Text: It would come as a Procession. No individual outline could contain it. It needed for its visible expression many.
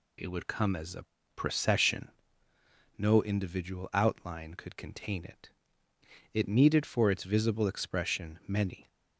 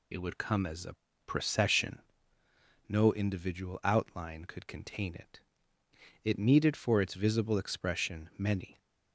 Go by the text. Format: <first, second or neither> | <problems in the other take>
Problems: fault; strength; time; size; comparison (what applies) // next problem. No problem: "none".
first | loses the start of "It"; at 0.1 s; 25 ms // pauses between "a" and "Procession"; slight; at 0.9 s; 0.32 s long; slight in the first